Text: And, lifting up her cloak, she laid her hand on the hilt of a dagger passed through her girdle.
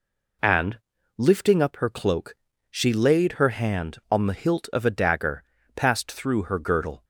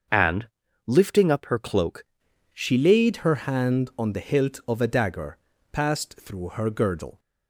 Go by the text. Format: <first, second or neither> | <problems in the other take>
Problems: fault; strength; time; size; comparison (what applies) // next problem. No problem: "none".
first | starts louder than the rest; until 1.4 s; 6.5 dB // changes voice at "she"; from 2.5 s on; 4.6 s long // pauses between "dagger" and "passed"; slight; at 5.3 s; 0.36 s long; slight in the first